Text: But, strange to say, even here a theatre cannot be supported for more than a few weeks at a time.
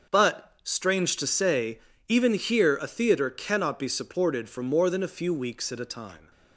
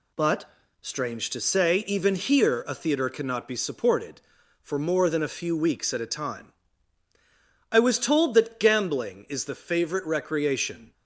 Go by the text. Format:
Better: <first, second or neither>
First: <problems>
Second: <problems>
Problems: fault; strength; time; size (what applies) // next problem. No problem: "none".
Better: first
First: none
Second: goes on to say "I was told that gambling is the favourite recreation"; strong; from 7.7 s on; 3.2 s long